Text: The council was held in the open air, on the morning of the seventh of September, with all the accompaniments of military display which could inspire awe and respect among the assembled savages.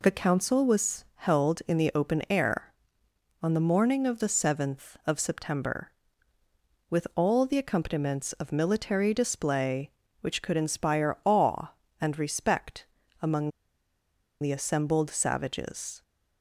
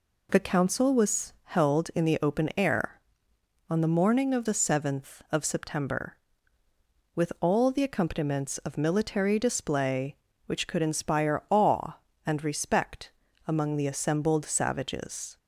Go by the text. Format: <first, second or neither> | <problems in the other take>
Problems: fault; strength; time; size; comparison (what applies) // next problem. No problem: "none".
second | pauses between "respect" and "among"; slight; at 12.8 s; 0.36 s long; slight in the second // pauses between "among" and "the"; noticeable; at 13.5 s; 0.91 s long